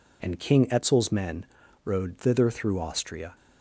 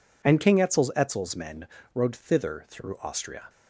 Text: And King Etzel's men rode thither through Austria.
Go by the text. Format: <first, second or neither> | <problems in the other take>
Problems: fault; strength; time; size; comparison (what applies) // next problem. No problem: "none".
first | says "Etzel's" twice; at 0.9 s // pauses between "men" and "rode"; slight; at 1.6 s; 0.26 s long; slight in the first